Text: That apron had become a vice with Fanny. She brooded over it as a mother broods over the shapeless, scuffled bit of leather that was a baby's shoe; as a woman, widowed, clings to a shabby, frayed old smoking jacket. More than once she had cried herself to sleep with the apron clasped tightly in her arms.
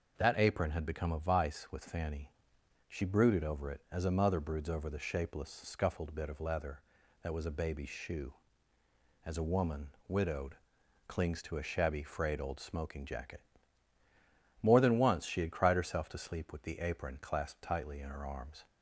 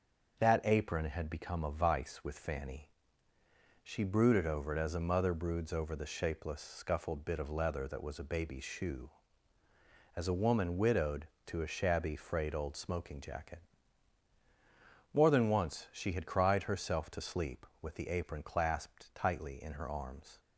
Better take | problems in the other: first | starts louder than the rest; until 1.4 s; 7 dB // skips "clings"; at 11.3 s

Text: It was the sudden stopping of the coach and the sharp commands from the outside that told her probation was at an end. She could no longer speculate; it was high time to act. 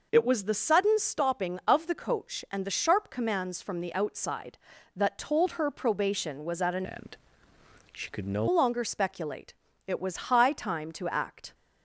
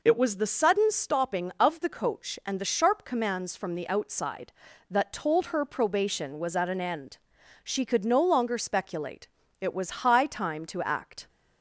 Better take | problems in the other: second | changes voice from "end" to "no"; from 6.8 to 8.4 s; 1.6 s long

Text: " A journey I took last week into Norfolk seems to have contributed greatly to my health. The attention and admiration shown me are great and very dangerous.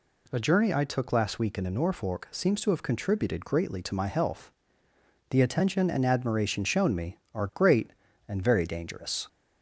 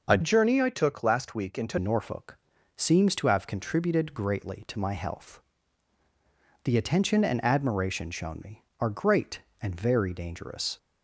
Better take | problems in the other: first | changes voice from "journey" to "into"; from 0.2 to 1.7 s; 1.5 s long // pauses between "Norfolk" and "seems"; at 2.3 s; 0.38 s long

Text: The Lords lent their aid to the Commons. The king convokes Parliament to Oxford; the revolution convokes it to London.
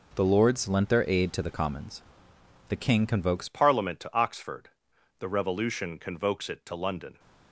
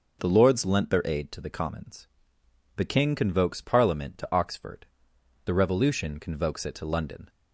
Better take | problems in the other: second | changes voice at "Parliament"; from 3.4 s on; 3.7 s long

